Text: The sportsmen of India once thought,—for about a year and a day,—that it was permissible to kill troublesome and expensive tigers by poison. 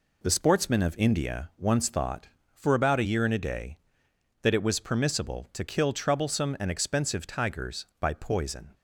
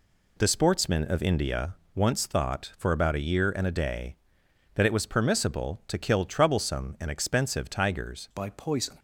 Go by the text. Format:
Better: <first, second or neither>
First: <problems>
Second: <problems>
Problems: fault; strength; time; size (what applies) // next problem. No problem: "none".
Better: first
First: none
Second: pauses between "India" and "once"; slight; at 1.7 s; 0.22 s long // changes voice at "by"; from 8.3 s on; 0.6 s long